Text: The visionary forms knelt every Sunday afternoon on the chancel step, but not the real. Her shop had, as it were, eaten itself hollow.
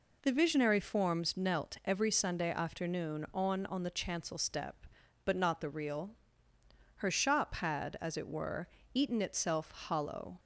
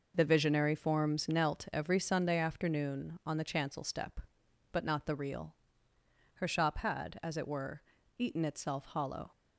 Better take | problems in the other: second | says "on" twice; at 3.6 s

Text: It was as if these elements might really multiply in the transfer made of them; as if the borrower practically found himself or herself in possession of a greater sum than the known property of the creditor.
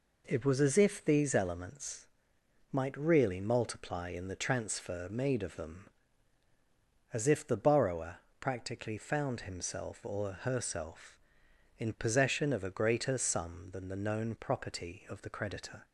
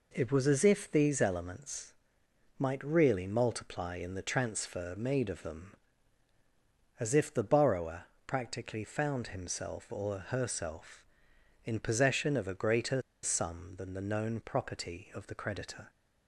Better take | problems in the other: first | pauses between "elements" and "might"; noticeable; at 1.9 s; 0.64 s long; noticeable in the first // pauses between "borrower" and "practically"; slight; at 8.0 s; 0.22 s long; slight in the first // pauses between "greater" and "sum"; slight; at 13.0 s; 0.23 s long

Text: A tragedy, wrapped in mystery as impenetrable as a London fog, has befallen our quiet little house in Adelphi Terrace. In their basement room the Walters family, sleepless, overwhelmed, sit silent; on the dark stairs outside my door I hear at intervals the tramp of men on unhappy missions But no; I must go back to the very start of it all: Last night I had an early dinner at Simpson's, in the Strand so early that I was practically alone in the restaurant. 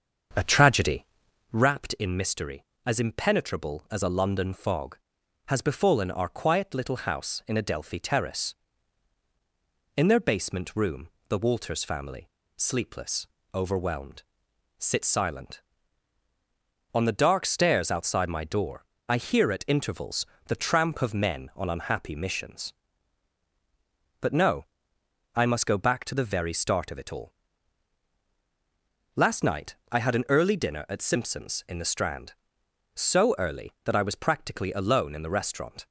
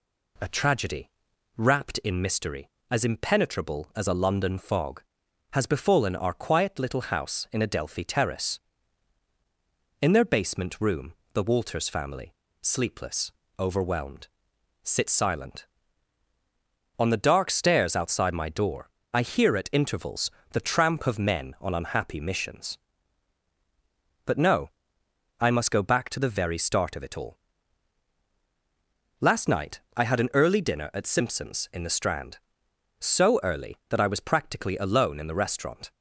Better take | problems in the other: second | starts louder than the rest; until 1.7 s; 7 dB // pauses between "room" and "the"; slight; at 11.0 s; 0.18 s long; slight in the second // pauses between "door" and "I"; slight; at 18.8 s; 0.26 s long; slight in the second // pauses between "intervals" and "the"; slight; at 20.2 s; 0.20 s long; slight in the second // pauses between "night" and "I"; slight; at 29.7 s; 0.16 s long; slight in the second

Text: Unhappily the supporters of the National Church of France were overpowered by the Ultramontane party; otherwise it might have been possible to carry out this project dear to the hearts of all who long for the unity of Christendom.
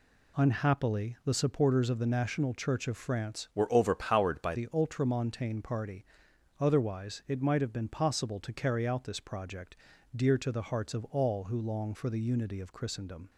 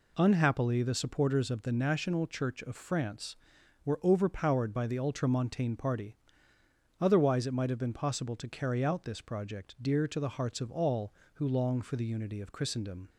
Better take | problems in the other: second | changes voice from "were" to "by"; from 3.5 to 4.5 s; 1.0 s long // pauses between "project" and "dear"; at 9.7 s; 0.38 s long

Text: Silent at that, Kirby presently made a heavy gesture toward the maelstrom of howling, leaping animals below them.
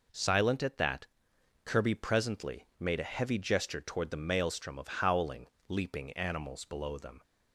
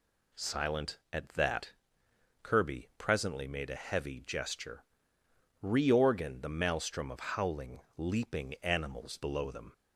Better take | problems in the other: first | says "reorgan" for "toward"; at 5.6 s

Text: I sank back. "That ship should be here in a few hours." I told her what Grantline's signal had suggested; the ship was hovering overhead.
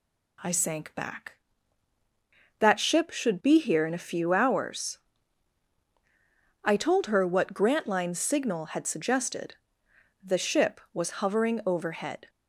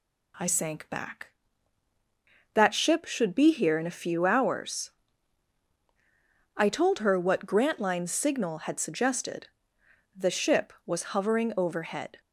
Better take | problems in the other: neither | none

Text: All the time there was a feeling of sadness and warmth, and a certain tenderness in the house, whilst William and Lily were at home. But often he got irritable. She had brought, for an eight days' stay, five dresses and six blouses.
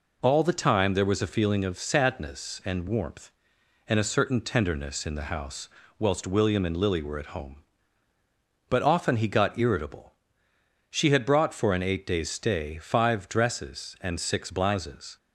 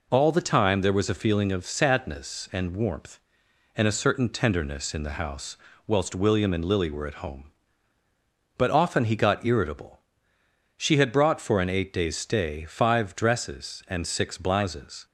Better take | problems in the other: neither | none

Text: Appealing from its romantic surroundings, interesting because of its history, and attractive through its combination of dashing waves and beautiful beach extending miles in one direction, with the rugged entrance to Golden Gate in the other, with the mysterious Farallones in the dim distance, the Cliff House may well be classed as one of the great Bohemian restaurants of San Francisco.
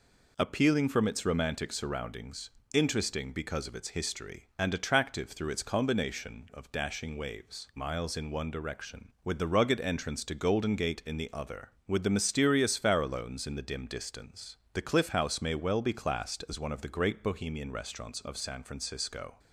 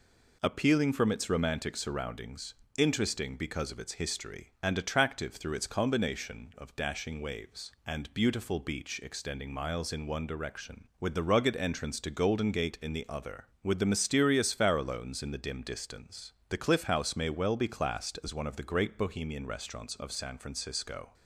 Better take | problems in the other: second | skips "and beautiful beach extending"; at 7.7 s

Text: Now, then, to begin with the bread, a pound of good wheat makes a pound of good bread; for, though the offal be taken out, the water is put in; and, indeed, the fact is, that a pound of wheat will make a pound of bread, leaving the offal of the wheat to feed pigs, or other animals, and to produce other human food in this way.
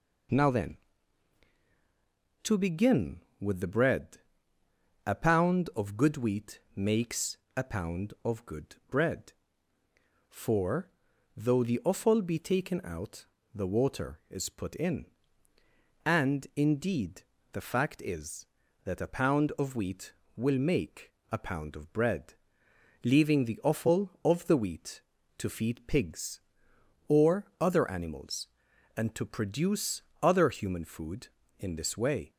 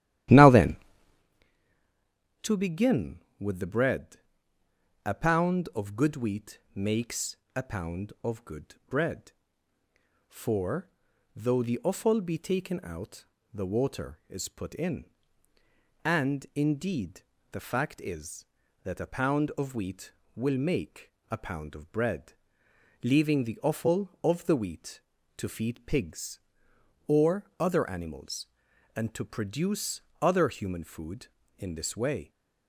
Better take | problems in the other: first | starts louder than the rest; strong; until 1.3 s; 13.5 dB // pauses between "wheat" and "makes"; slight; at 6.5 s; 0.16 s long; slight in the first // pauses between "makes" and "a"; slight; at 7.3 s; 0.20 s long; slight in the first // pauses between "make" and "a"; slight; at 21.1 s; 0.20 s long; slight in the first // pauses between "produce" and "other"; slight; at 30.0 s; 0.20 s long; slight in the first

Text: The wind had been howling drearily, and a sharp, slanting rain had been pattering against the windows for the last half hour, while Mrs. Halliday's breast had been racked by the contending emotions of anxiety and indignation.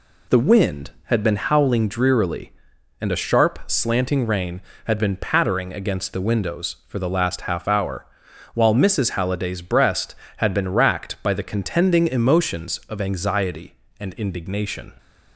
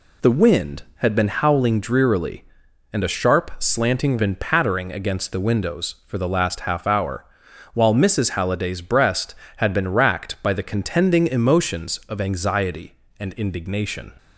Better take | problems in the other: first | skips "rain had"; at 4.1 s

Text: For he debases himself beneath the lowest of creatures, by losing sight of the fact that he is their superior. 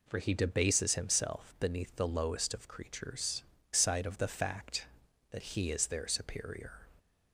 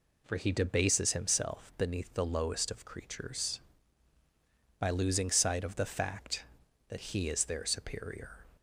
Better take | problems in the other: second | skips "by losing"; at 3.5 s

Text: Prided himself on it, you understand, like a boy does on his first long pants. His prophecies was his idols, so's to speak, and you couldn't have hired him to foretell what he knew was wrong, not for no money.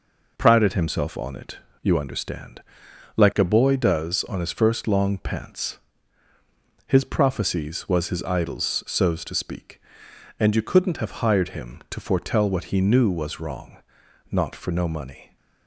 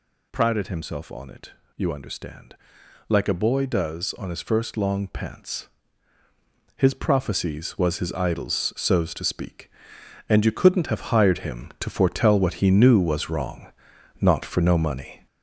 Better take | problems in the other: first | gets louder; noticeable; throughout; 6 dB

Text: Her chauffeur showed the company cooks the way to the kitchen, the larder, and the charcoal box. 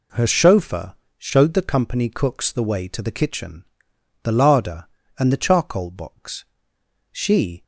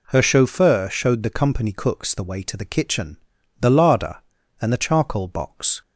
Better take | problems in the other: second | pauses between "chauffeur" and "showed"; slight; at 0.9 s; 0.22 s long // goes on to say "She"; from 7.1 s on; 0.52 s long

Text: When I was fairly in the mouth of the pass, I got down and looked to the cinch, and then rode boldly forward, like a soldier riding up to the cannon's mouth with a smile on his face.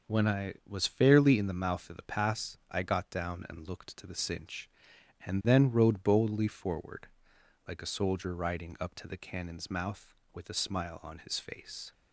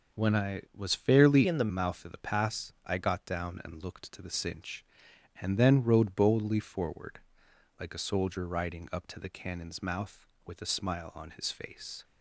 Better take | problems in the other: first | starts louder than the rest; noticeable; until 1.2 s; 6 dB; noticeable in the first // changes voice from "in" to "the"; from 1.4 to 1.7 s; 0.3 s long

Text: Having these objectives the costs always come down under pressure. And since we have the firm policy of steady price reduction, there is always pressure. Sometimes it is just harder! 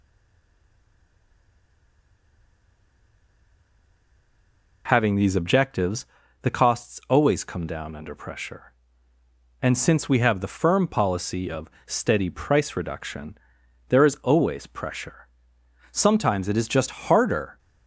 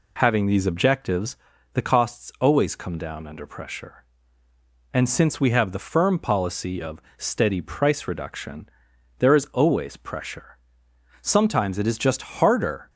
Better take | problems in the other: second | stays silent before the first word; strong; until 4.8 s; 4.8 s long // pauses between "objectives" and "the"; at 6.0 s; 0.37 s long; also in the second // pauses between "of" and "steady"; slight; at 11.7 s; 0.16 s long; slight in the second // pauses between "just" and "harder"; slight; at 16.8 s; 0.19 s long; slight in the second

